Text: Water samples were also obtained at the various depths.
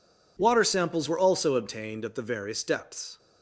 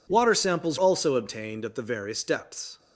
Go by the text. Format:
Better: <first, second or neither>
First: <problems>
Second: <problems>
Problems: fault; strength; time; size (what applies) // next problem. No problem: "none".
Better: first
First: none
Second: skips "were"; at 0.7 s